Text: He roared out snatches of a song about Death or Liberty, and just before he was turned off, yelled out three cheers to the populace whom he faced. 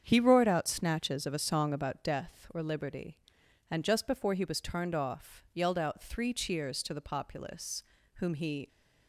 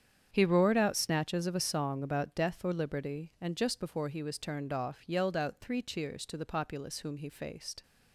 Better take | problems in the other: second | starts louder than the rest; strong; until 1.0 s; 8 dB; strong in the second // pauses between "populace" and "whom"; slight; at 7.8 s; 0.34 s long // stops before "faced"; at 8.6 s

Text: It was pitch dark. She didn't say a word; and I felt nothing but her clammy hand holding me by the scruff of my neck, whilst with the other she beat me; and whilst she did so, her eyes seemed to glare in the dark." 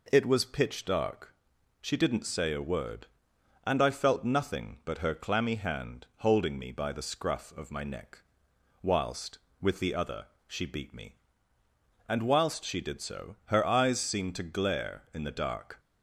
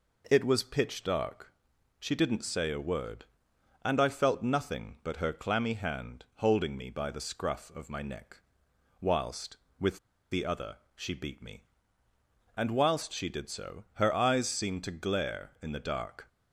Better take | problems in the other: first | pauses between "with" and "the"; slight; at 9.9 s; 0.33 s long // pauses between "other" and "she"; slight; at 10.7 s; 0.18 s long; slight in the first

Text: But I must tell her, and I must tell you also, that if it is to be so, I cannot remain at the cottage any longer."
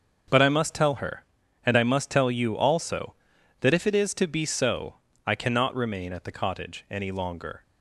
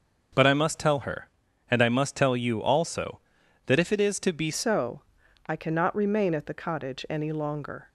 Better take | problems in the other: first | starts louder than the rest; noticeable; until 1.7 s; 6 dB; also in the first // changes voice at "so"; from 4.5 s on; 3.3 s long

